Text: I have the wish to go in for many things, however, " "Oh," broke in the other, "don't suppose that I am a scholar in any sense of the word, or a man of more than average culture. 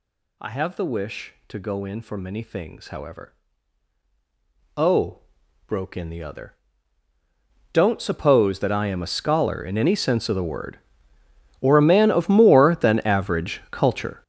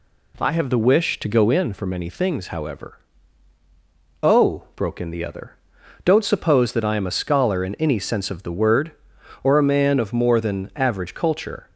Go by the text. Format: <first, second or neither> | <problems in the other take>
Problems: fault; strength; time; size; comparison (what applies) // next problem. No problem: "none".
second | gets louder; strong; throughout; 20 dB